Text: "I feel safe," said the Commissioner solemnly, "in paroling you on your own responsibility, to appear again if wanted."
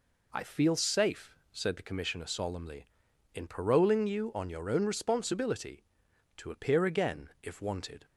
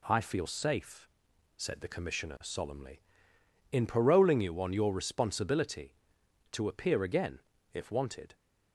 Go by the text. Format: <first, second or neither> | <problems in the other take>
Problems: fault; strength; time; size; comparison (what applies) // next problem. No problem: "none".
first | skips "own"; at 4.9 s // pauses between "again" and "if"; slight; at 7.4 s; 0.32 s long